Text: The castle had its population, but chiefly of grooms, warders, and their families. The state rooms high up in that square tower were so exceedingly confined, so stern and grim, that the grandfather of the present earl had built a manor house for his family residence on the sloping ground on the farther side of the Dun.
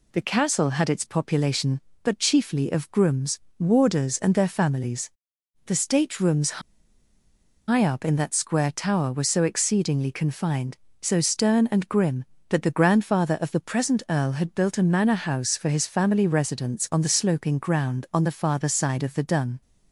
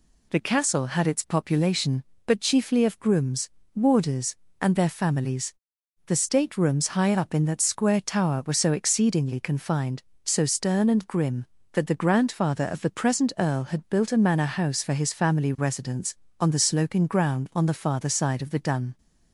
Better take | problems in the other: second | pauses between "rooms" and "high"; at 6.6 s; 1.0 s long

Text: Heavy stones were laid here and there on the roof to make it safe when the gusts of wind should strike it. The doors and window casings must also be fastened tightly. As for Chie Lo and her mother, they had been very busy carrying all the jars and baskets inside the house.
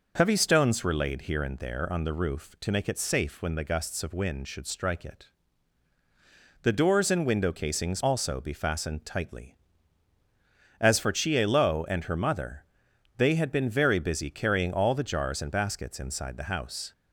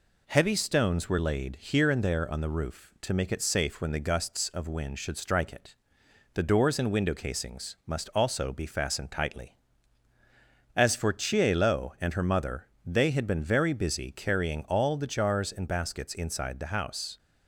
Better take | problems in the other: second | skips "must"; at 8.0 s

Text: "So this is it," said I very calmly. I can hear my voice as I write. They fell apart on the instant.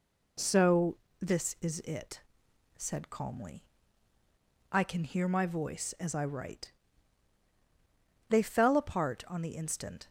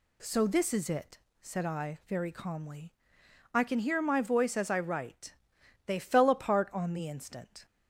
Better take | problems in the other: second | pauses between "So" and "this"; slight; at 0.9 s; 0.22 s long // skips "I very"; at 3.1 s

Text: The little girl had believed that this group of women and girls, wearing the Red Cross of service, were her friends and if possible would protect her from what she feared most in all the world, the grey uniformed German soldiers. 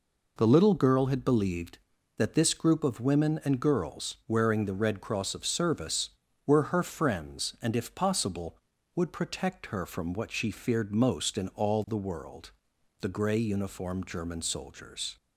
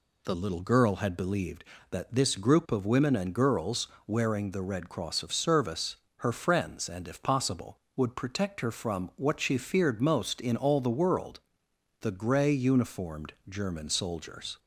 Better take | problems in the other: first | skips "were"; at 6.0 s // pauses between "uniformed" and "German"; slight; at 13.3 s; 0.16 s long

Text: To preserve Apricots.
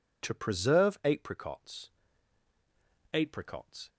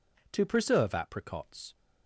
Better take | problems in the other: second | says "Apricots" twice; at 3.1 s

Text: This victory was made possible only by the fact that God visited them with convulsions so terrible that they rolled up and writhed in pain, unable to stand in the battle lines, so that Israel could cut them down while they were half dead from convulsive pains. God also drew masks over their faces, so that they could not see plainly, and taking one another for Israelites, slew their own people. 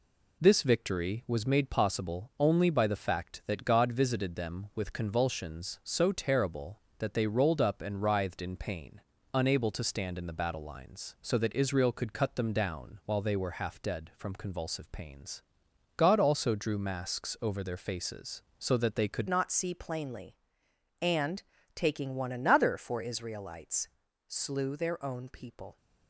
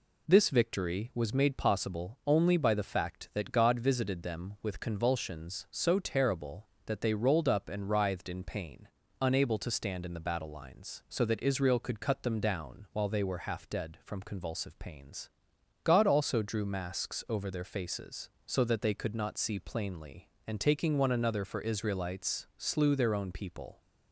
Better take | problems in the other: second | changes voice at "not"; from 19.2 s on; 6.5 s long // pauses between "and" and "taking"; slight; at 21.4 s; 0.34 s long

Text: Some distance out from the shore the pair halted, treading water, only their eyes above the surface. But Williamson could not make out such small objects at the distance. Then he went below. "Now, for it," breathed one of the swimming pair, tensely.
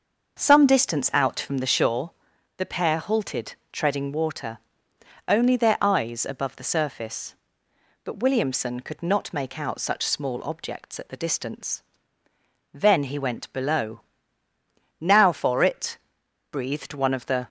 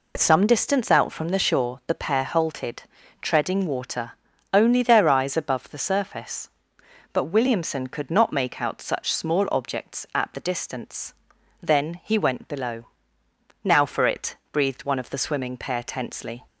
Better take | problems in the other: second | starts louder than the rest; until 1.4 s; 6.5 dB // pauses between "shore" and "the"; noticeable; at 2.1 s; 0.46 s long // stops before "swimming pair tensely"; at 17.4 s

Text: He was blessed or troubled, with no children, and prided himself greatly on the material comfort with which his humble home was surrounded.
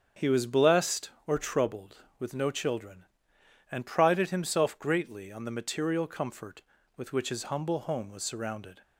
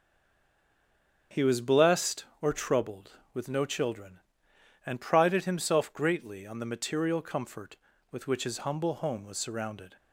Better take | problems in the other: first | stays silent before the first word; noticeable; until 1.3 s; 1.3 s long // starts louder than the rest; strong; until 2.4 s; 7.5 dB; strong in the first

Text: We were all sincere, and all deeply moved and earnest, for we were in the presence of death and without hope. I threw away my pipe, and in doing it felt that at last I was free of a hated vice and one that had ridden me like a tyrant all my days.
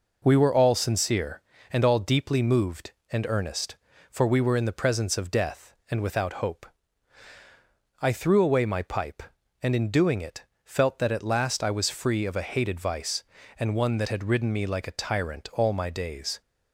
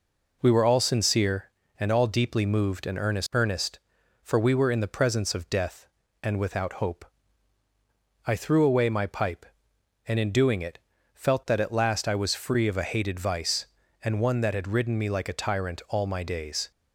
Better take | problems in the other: first | says "earnest" twice; at 3.3 s // pauses between "it" and "felt"; slight; at 10.7 s; 0.34 s long; slight in the first

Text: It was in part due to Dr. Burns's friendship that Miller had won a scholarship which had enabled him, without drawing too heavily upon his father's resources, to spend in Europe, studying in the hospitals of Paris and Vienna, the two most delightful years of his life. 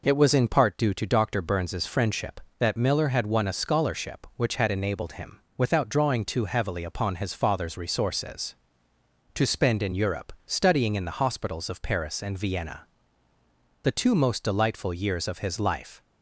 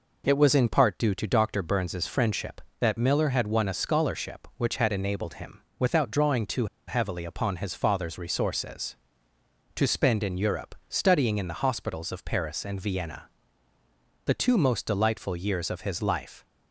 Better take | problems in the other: first | pauses between "too" and "heavily"; slight; at 6.6 s; 0.22 s long

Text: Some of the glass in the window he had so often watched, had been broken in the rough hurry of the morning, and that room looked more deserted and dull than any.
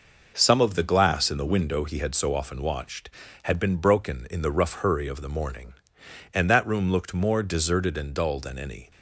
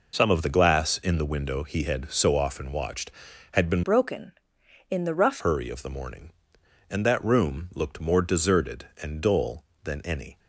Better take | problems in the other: first | changes voice from "broken" to "rough"; from 3.8 to 5.3 s; 1.5 s long

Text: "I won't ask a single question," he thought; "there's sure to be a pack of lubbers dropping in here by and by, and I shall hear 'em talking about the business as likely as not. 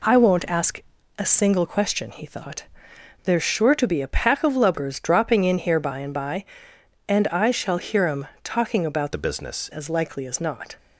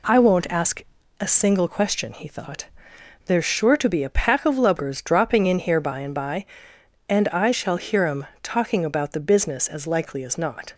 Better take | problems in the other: second | pauses between "ask" and "a"; slight; at 0.8 s; 0.36 s long; slight in the second // pauses between "em" and "talking"; slight; at 8.2 s; 0.16 s long; slight in the second // changes voice from "the" to "business"; from 9.1 to 9.7 s; 0.6 s long

